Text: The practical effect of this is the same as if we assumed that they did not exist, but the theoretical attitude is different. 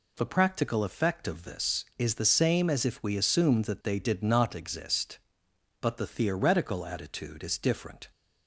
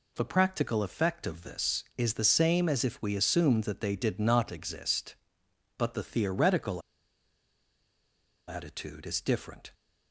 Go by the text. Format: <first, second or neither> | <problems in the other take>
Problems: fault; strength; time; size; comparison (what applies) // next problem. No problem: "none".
first | pauses between "theoretical" and "attitude"; strong; at 6.8 s; 1.6 s long